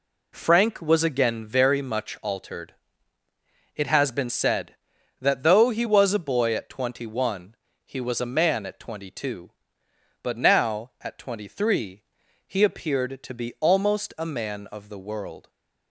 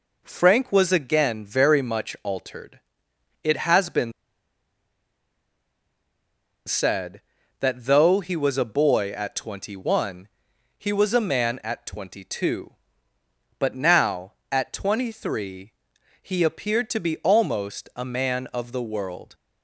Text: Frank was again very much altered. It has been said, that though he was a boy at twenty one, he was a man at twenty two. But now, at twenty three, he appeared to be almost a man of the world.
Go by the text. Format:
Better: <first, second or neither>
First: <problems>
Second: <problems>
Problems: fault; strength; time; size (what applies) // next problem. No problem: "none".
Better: first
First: none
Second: pauses between "been" and "said"; strong; at 4.1 s; 2.5 s long